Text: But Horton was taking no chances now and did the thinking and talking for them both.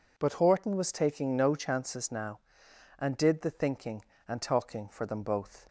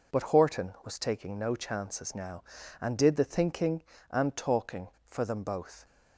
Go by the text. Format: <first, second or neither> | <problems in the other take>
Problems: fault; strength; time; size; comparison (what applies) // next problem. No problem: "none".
neither | none